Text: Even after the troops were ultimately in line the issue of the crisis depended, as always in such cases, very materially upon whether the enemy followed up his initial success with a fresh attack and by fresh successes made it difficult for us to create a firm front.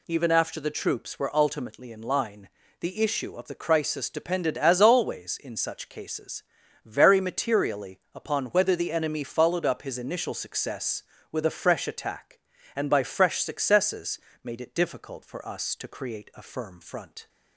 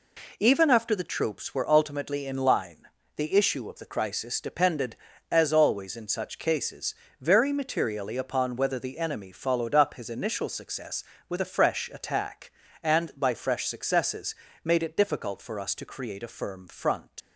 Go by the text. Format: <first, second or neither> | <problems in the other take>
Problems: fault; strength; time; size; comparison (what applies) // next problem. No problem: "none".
first | pauses between "line" and "the"; slight; at 2.8 s; 0.28 s long; slight in the first // pauses between "successes" and "made"; slight; at 14.3 s; 0.28 s long; slight in the first // leaves "front" unfinished; at 17.2 s; 115 ms